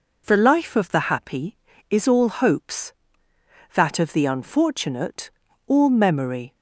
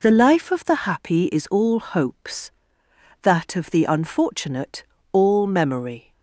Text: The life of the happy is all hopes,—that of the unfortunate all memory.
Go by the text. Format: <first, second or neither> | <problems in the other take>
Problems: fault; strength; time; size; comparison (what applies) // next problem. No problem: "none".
neither | pauses between "unfortunate" and "all"; the same in both